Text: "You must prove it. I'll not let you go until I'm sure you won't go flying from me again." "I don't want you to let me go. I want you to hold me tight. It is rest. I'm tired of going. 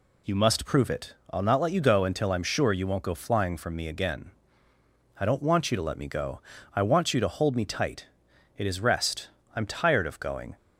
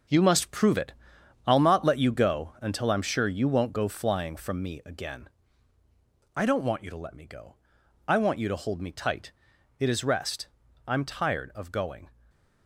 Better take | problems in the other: first | gets quieter; strong; throughout; 9 dB // stays silent after the last word; slight; from 12.1 s on; 0.5 s long

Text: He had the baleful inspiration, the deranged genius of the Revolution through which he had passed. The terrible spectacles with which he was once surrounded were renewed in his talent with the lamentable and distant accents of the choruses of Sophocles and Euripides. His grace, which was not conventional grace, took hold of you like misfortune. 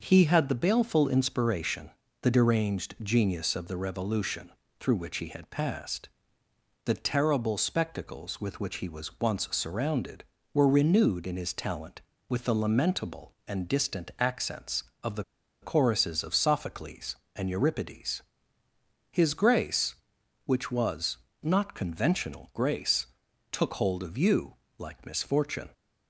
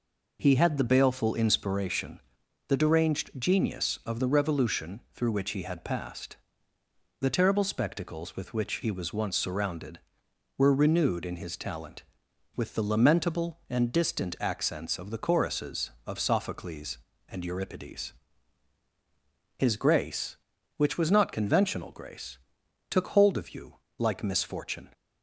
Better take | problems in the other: second | starts louder than the rest; noticeable; until 1.0 s; 6 dB // pauses between "Revolution" and "through"; slight; at 4.4 s; 0.30 s long // pauses between "the" and "choruses"; at 15.2 s; 0.38 s long // pauses between "was" and "not"; slight; at 21.1 s; 0.26 s long // pauses between "you" and "like"; slight; at 24.5 s; 0.24 s long; slight in the second

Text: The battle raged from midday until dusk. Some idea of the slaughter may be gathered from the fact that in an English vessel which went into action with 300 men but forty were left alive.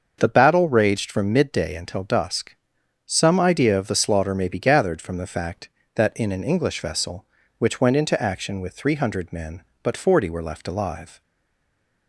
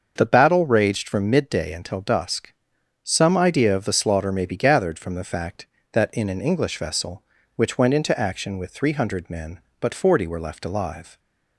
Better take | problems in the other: second | starts louder than the rest; until 1.2 s; 6.5 dB; also in the second // stays silent after the last word; slight; from 11.2 s on; 0.8 s long

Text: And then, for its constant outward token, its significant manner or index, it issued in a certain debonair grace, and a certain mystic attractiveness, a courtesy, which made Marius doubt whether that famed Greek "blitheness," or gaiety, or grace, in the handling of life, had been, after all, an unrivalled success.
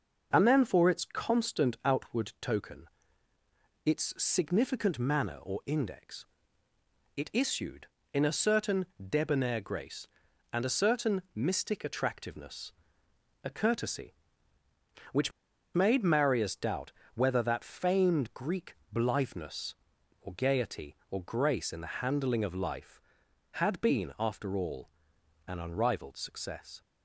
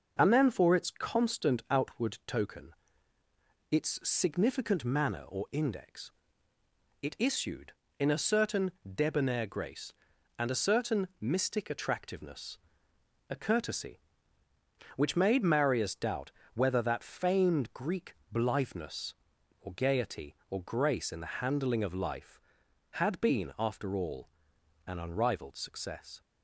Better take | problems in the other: second | pauses between "certain" and "debonair"; slight; at 8.8 s; 0.24 s long; slight in the second // pauses between "which" and "made"; at 15.3 s; 0.43 s long // pauses between "doubt" and "whether"; slight; at 16.9 s; 0.22 s long; slight in the second // pauses between "Greek" and "blitheness"; slight; at 18.7 s; 0.16 s long; slight in the second

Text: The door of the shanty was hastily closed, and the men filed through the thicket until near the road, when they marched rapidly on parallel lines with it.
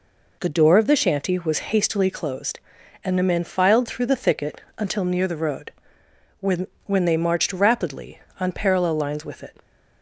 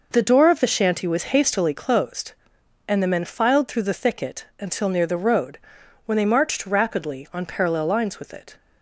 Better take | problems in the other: second | pauses between "thicket" and "until"; slight; at 4.6 s; 0.16 s long; slight in the second // says "when" twice; at 6.8 s

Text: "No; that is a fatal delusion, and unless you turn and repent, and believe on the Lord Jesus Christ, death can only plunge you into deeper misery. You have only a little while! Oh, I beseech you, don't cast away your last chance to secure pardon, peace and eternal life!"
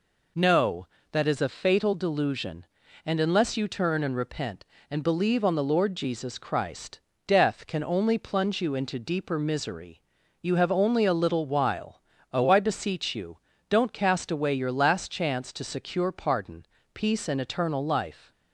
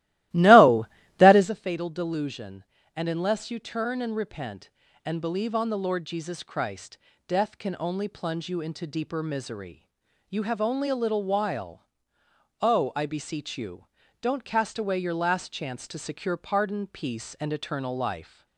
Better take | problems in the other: first | starts louder than the rest; strong; until 1.5 s; 16 dB

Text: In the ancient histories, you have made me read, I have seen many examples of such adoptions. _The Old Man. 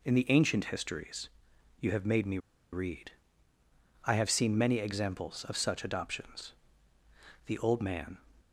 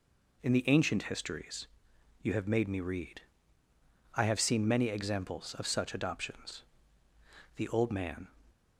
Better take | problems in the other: second | pauses between "me" and "read"; slight; at 2.3 s; 0.33 s long

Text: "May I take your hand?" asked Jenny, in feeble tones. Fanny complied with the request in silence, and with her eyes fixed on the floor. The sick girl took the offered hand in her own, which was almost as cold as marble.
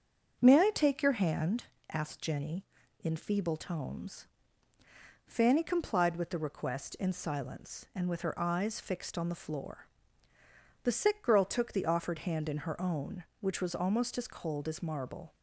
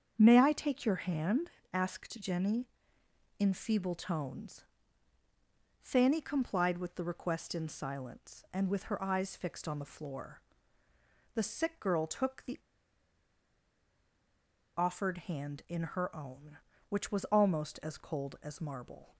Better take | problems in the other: first | starts louder than the rest; strong; until 1.1 s; 7 dB; also in the first // pauses between "the" and "offered"; strong; at 12.5 s; 2.1 s long

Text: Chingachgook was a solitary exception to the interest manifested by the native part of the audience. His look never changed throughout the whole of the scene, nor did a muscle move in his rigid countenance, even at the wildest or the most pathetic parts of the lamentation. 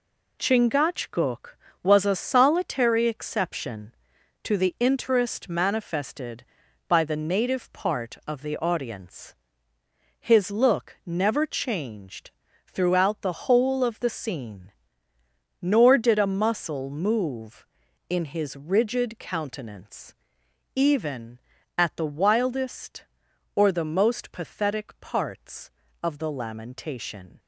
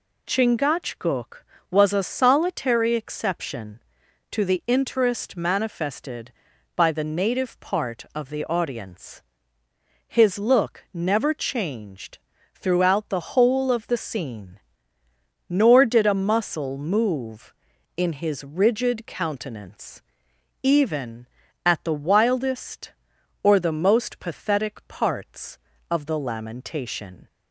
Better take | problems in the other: second | gets quieter; throughout; 6.5 dB // pauses between "changed" and "throughout"; slight; at 12.3 s; 0.36 s long; slight in the second

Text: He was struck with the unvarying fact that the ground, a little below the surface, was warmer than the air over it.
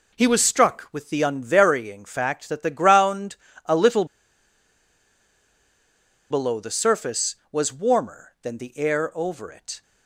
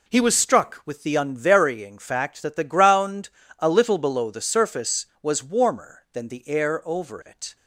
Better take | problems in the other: second | pauses between "little" and "below"; strong; at 4.0 s; 2.2 s long

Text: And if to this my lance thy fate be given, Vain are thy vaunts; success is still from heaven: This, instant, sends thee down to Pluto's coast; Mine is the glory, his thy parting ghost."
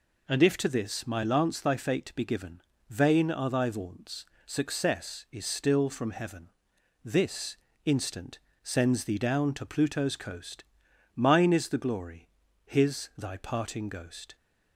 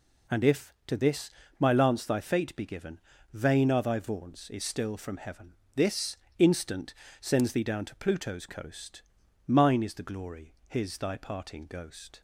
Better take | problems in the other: first | pauses between "this" and "my"; slight; at 1.2 s; 0.30 s long // skips "success"; at 4.4 s

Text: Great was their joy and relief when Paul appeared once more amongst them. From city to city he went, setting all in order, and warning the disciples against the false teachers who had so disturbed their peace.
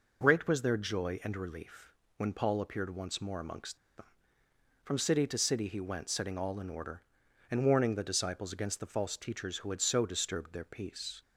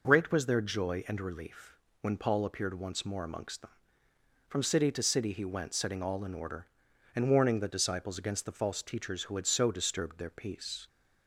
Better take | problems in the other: second | pauses between "relief" and "when"; slight; at 1.8 s; 0.28 s long; slight in the second // pauses between "amongst" and "them"; slight; at 3.7 s; 0.19 s long

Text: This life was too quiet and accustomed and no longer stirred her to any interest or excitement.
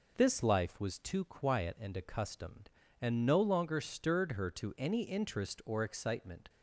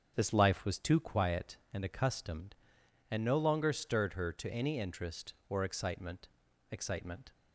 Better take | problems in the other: first | starts louder than the rest; until 1.1 s; 7 dB // says "excitement" twice; at 6.7 s

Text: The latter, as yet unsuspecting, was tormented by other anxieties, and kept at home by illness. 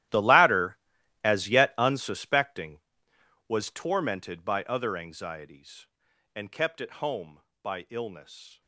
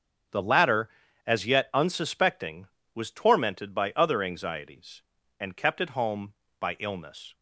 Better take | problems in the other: second | gets quieter; strong; throughout; 17.5 dB // starts louder than the rest; strong; until 1.5 s; 13.5 dB; also in the second

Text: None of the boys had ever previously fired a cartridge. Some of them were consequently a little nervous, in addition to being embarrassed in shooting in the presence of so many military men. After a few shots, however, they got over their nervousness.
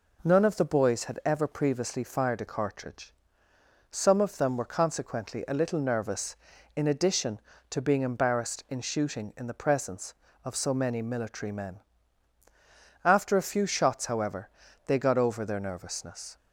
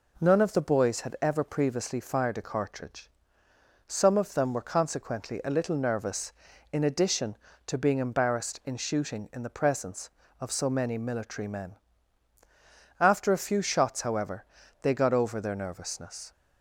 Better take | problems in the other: neither | none

